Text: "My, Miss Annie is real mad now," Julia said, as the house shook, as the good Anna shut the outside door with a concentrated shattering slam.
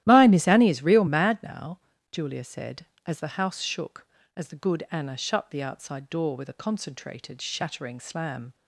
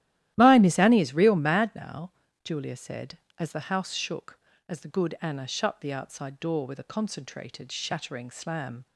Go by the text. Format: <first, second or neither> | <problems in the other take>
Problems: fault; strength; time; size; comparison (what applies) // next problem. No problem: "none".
neither | starts louder than the rest; strong; the same in both